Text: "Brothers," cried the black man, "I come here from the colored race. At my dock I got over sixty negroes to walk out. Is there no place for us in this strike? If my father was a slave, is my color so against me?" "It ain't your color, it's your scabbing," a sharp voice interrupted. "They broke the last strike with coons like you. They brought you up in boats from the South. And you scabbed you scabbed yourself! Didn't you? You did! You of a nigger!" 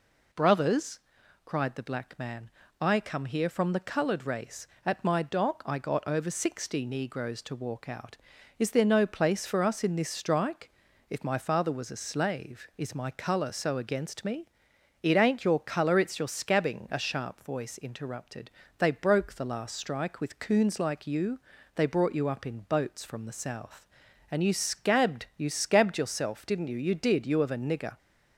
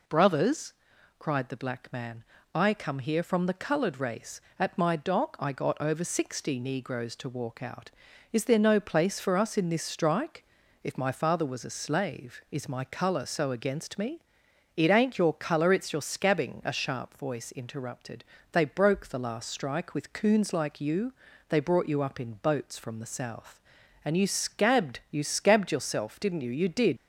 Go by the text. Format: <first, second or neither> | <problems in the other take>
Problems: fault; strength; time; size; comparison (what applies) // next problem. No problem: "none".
first | stops before "You of a nigger"; at 26.9 s